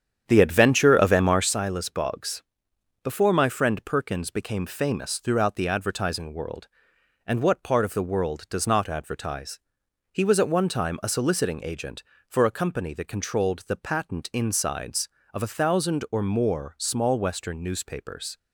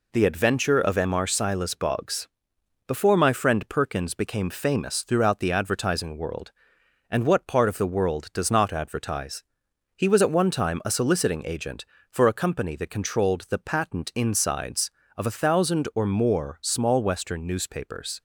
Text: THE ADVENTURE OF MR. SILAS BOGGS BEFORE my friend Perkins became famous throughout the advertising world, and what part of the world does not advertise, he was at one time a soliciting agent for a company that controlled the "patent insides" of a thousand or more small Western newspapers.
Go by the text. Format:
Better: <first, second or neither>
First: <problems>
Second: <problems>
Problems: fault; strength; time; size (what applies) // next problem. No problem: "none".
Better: second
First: starts louder than the rest; strong; until 1.5 s; 8.5 dB // pauses between "BOGGS" and "BEFORE"; noticeable; at 2.4 s; 0.62 s long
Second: pauses between "BOGGS" and "BEFORE"; noticeable; at 2.2 s; 0.60 s long